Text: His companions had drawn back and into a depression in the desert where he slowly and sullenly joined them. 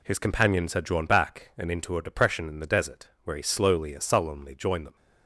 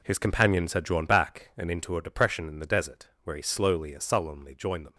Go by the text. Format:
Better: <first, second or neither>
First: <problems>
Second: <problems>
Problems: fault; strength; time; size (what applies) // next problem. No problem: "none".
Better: first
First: pauses between "desert" and "where"; slight; at 3.0 s; 0.16 s long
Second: gets quieter; strong; throughout; 9.5 dB // pauses between "desert" and "where"; slight; at 3.0 s; 0.16 s long